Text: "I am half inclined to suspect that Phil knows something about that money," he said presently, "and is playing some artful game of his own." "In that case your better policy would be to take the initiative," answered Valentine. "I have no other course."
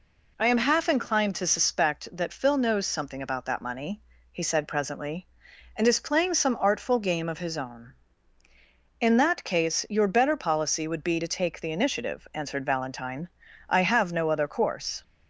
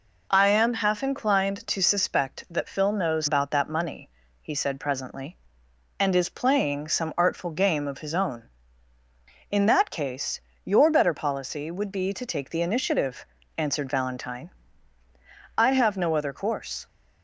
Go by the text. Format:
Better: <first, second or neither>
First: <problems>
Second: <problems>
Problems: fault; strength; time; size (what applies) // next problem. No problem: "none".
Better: first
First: none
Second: skips "something"; at 3.2 s // pauses between "case" and "your"; slight; at 10.3 s; 0.24 s long